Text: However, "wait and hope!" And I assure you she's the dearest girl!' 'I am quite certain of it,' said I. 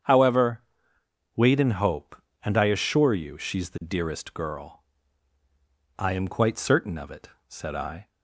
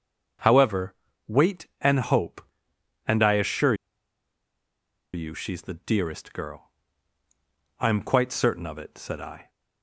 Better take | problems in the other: first | starts louder than the rest; until 1.9 s; 7 dB; strong in the first // pauses between "assure" and "you"; strong; at 3.7 s; 1.3 s long

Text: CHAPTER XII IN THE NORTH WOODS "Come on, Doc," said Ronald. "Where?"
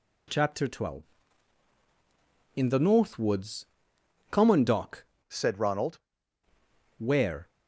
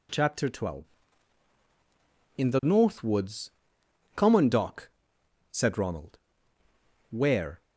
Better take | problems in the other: second | pauses between "WOODS" and "Come"; noticeable; at 3.6 s; 0.64 s long; noticeable in the second // changes voice from "said" to "Ronald"; from 5.2 to 5.9 s; 0.7 s long

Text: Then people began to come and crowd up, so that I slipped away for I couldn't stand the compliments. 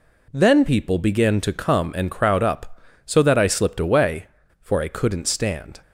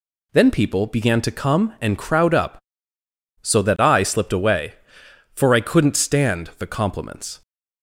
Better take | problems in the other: second | stops before "the compliments"; at 5.8 s

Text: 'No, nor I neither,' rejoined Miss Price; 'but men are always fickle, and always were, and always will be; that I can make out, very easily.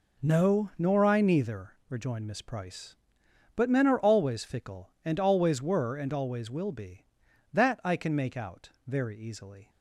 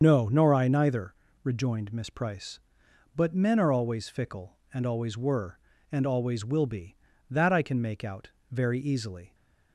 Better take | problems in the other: first | loses the start of "No"; at 0.0 s; 40 ms // starts louder than the rest; until 1.0 s; 7 dB

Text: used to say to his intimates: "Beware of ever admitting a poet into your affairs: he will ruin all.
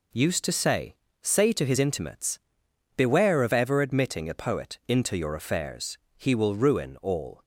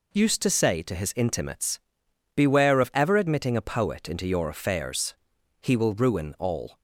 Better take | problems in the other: second | says "say" twice; at 1.2 s

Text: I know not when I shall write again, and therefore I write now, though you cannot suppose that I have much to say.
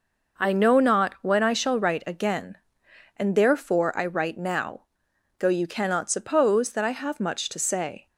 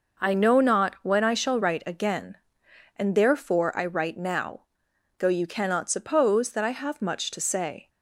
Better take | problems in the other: neither | none

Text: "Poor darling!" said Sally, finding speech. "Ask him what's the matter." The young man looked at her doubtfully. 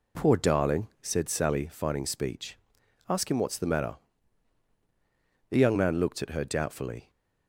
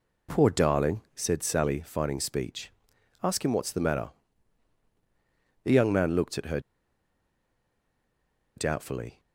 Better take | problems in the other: first | pauses between "her" and "doubtfully"; strong; at 6.5 s; 1.9 s long

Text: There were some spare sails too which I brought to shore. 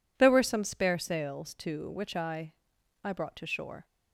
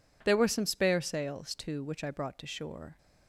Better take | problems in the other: second | says "I" twice; at 3.0 s

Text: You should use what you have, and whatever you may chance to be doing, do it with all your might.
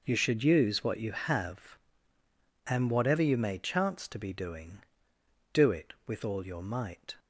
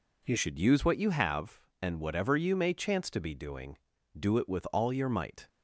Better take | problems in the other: first | changes voice at "should"; from 0.3 s on; 5.1 s long

